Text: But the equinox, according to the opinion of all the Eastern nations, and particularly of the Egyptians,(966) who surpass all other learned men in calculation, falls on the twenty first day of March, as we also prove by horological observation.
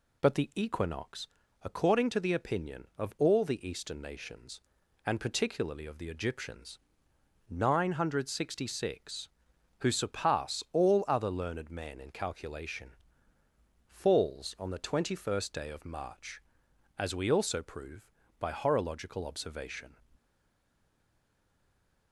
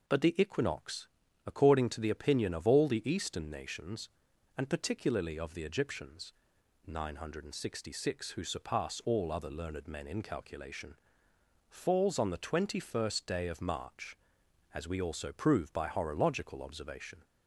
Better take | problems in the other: second | stays silent after the last word; noticeable; from 20.1 s on; 2.0 s long

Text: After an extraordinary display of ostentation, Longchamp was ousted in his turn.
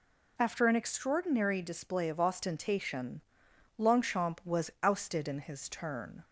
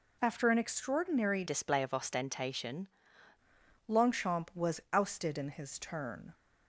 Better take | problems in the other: first | changes voice from "display" to "ostentation"; from 1.4 to 2.8 s; 1.4 s long

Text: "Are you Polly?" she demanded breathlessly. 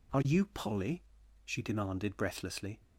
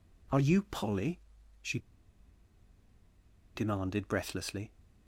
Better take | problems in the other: first | pauses between "she" and "demanded"; strong; at 1.7 s; 1.7 s long

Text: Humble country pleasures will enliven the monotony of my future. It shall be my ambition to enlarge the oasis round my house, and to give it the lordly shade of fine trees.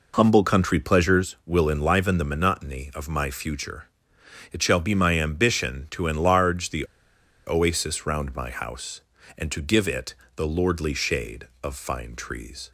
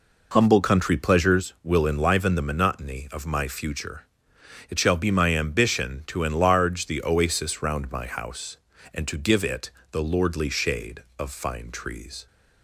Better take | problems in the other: second | pauses between "the" and "oasis"; noticeable; at 6.8 s; 0.60 s long // pauses between "it" and "the"; slight; at 10.1 s; 0.20 s long; slight in the second

